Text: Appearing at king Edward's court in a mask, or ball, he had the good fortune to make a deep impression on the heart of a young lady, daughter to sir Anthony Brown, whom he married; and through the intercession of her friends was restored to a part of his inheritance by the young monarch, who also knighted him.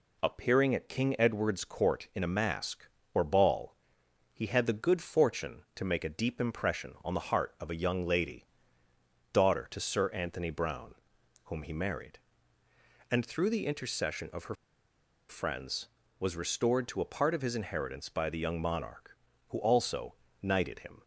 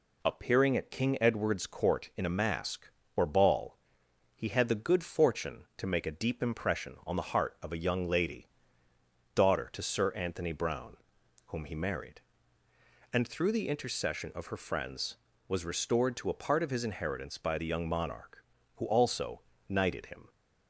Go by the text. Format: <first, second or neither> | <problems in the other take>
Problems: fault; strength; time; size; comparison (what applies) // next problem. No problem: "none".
second | pauses between "her" and "friends"; noticeable; at 14.5 s; 0.74 s long // pauses between "also" and "knighted"; slight; at 20.1 s; 0.28 s long; slight in the second